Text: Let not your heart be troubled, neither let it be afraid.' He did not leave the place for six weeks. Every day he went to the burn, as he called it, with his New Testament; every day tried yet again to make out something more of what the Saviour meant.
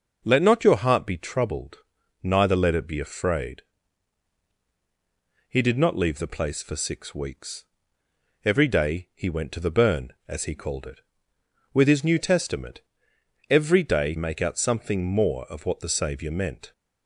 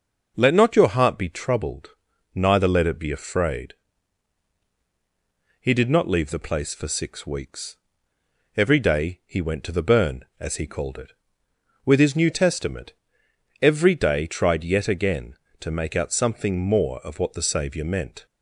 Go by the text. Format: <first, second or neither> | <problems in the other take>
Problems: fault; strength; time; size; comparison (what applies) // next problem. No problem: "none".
second | skips "tried yet again to"; at 14.1 s